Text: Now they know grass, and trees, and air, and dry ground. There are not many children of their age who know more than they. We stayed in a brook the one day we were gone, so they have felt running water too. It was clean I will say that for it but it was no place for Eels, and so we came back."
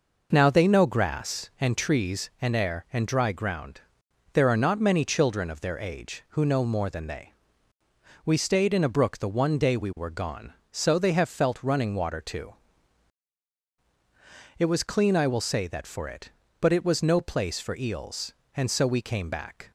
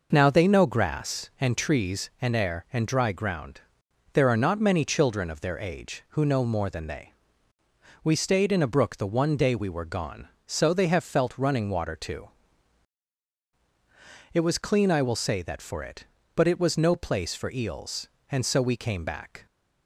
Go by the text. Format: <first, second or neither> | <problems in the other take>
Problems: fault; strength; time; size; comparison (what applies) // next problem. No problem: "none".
neither | none